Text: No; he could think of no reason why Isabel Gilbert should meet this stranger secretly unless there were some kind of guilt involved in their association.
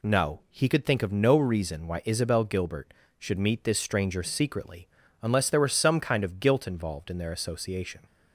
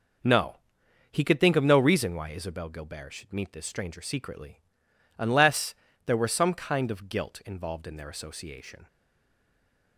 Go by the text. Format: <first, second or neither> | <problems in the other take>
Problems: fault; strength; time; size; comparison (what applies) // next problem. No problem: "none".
first | pauses between "secretly" and "unless"; noticeable; at 4.5 s; 0.58 s long; slight in the first // pauses between "unless" and "there"; slight; at 5.7 s; 0.32 s long // stays silent after the last word; from 8.8 s on; 1.1 s long